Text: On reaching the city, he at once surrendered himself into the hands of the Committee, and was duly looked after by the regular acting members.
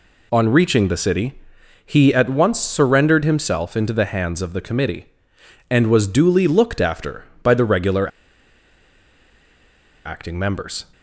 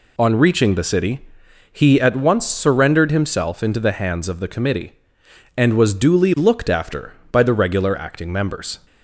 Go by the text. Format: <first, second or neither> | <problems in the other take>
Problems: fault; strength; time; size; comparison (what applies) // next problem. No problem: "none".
second | pauses between "regular" and "acting"; strong; at 8.0 s; 1.9 s long